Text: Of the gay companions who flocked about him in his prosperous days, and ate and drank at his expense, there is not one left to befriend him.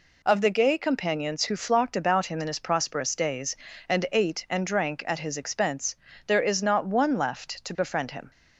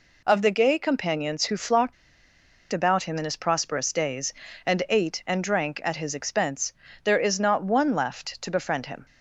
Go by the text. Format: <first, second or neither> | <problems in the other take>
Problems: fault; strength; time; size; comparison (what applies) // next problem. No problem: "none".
first | pauses between "flocked" and "about"; noticeable; at 1.9 s; 0.79 s long